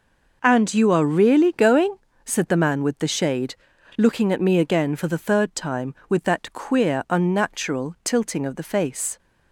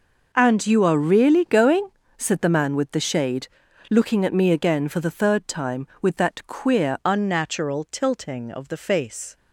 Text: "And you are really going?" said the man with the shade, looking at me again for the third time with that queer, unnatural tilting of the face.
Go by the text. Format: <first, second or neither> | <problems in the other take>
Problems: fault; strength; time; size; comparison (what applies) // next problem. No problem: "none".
first | changes voice at "unnatural"; from 7.0 s on; 2.3 s long